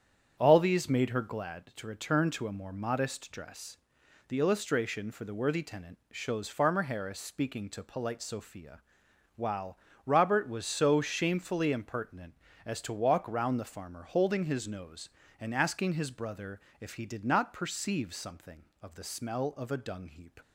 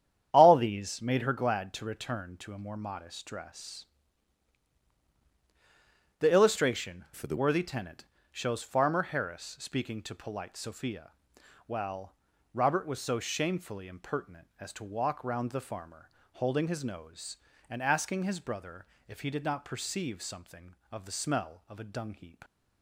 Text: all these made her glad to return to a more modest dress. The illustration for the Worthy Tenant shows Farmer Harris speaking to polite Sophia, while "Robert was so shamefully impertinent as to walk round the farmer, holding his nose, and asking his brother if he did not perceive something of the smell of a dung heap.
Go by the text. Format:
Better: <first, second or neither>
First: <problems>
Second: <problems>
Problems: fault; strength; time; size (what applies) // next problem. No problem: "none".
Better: first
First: starts louder than the rest; strong; until 1.3 s; 8 dB // pauses between "while" and "Robert"; slight; at 9.7 s; 0.30 s long // pauses between "brother" and "if"; slight; at 16.5 s; 0.21 s long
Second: starts louder than the rest; strong; until 1.3 s; 9.5 dB // changes voice from "for" to "the"; from 7.1 to 7.3 s; 0.2 s long // pauses between "Tenant" and "shows"; slight; at 8.0 s; 0.26 s long // pauses between "while" and "Robert"; at 12.1 s; 0.40 s long // pauses between "brother" and "if"; slight; at 18.8 s; 0.22 s long